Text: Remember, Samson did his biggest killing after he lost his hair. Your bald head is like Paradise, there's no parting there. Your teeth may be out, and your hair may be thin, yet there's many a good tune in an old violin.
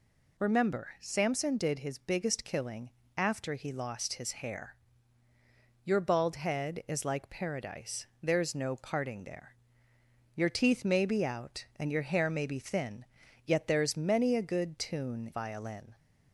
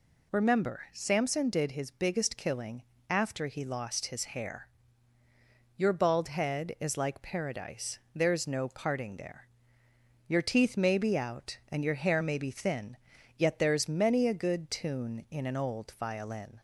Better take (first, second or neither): second